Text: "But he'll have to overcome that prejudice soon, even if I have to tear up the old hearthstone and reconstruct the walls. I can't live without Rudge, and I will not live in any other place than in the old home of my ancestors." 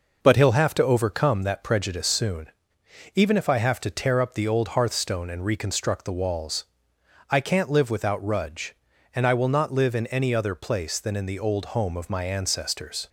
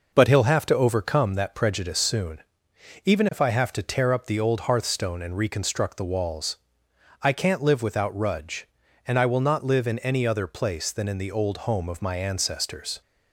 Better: neither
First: none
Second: none

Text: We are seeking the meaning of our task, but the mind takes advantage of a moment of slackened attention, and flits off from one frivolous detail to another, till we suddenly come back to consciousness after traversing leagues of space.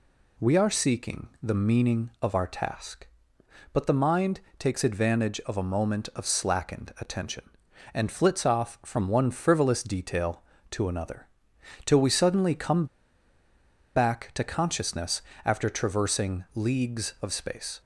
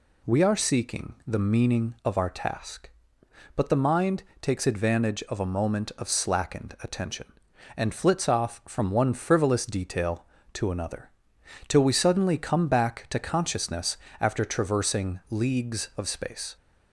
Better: second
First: pauses between "mind" and "takes"; slight; at 4.3 s; 0.20 s long // pauses between "come" and "back"; at 12.8 s; 1.1 s long // pauses between "consciousness" and "after"; slight; at 15.2 s; 0.24 s long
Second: pauses between "mind" and "takes"; slight; at 4.2 s; 0.20 s long // pauses between "consciousness" and "after"; slight; at 13.9 s; 0.24 s long

